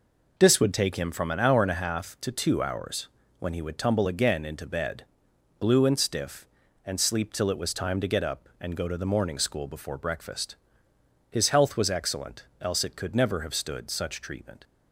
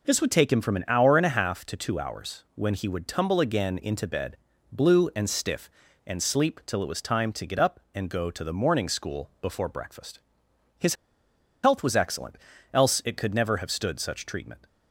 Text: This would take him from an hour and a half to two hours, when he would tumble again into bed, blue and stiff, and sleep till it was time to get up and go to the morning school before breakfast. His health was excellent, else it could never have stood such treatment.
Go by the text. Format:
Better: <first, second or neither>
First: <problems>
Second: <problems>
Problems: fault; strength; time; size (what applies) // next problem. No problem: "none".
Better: first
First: none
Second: pauses between "His" and "health"; noticeable; at 10.9 s; 0.69 s long